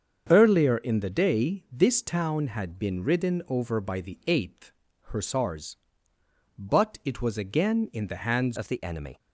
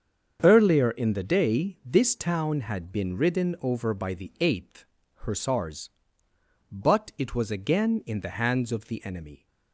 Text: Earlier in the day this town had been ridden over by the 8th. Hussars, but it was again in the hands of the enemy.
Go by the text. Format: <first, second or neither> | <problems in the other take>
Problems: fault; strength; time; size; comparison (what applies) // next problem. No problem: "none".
second | starts louder than the rest; until 1.3 s; 7 dB; also in the second // changes voice at "of"; from 8.5 s on; 0.6 s long